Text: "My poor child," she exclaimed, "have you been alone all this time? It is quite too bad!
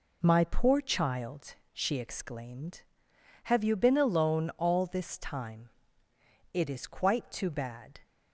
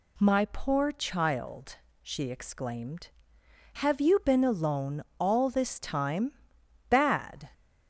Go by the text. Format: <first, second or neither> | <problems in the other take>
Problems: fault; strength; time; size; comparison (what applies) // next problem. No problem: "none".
first | pauses between "alone" and "all"; slight; at 5.0 s; 0.16 s long // skips "It is quite too"; at 6.6 s